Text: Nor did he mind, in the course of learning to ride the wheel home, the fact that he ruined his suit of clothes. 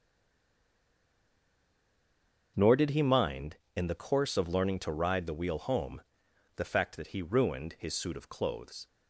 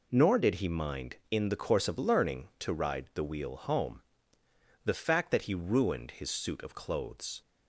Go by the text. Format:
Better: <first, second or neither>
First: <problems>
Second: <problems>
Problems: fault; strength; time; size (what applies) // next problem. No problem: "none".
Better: second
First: stays silent before the first word; strong; until 2.5 s; 2.5 s long // starts louder than the rest; until 3.5 s; 6.5 dB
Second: none